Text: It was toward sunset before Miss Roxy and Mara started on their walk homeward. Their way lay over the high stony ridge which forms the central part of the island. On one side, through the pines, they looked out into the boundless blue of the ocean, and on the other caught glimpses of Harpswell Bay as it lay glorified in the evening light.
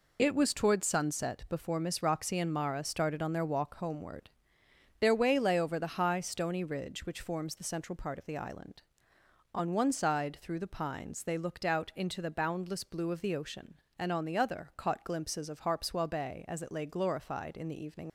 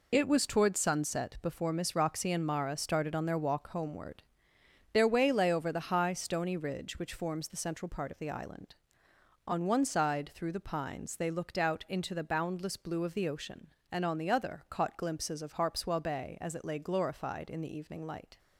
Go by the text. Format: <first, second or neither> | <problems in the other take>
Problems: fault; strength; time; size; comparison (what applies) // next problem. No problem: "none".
second | stops before "light"; at 18.0 s